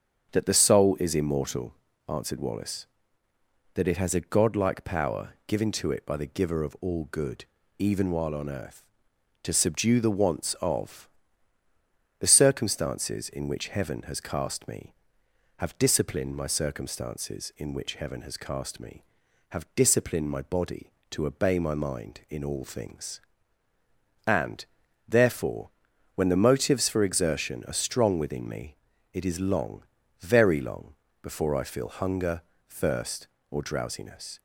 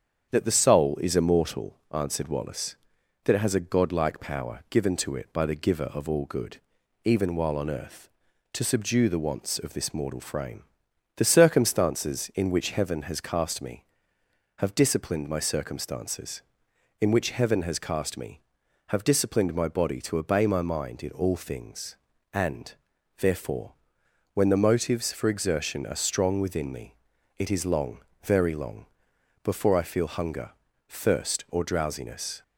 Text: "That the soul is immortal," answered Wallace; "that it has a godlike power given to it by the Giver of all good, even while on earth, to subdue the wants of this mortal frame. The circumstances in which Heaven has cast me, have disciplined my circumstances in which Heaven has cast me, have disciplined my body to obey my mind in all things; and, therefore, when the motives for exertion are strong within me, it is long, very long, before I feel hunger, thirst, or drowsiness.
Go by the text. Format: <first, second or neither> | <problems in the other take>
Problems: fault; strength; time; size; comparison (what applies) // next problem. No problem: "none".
second | starts louder than the rest; until 1.3 s; 7 dB; strong in the second // skips "this mortal frame"; at 11.6 s